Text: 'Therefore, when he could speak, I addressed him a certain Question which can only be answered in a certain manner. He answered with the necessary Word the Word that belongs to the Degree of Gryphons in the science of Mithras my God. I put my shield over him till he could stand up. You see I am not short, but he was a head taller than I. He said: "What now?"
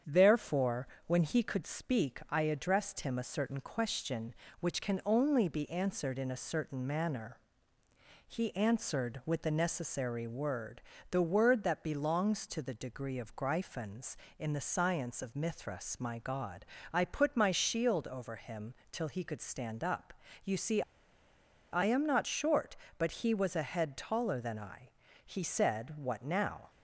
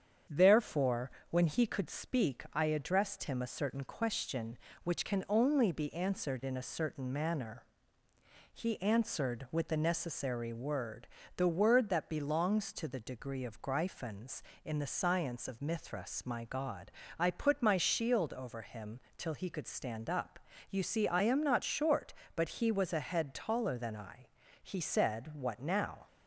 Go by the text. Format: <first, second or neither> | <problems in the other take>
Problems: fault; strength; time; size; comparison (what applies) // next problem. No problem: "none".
second | starts louder than the rest; strong; until 1.2 s; 8 dB; strong in the second // pauses between "Word" and "the"; slight; at 10.8 s; 0.28 s long; slight in the second // pauses between "him" and "till"; slight; at 18.7 s; 0.16 s long; slight in the second // pauses between "see" and "I"; noticeable; at 20.8 s; 0.89 s long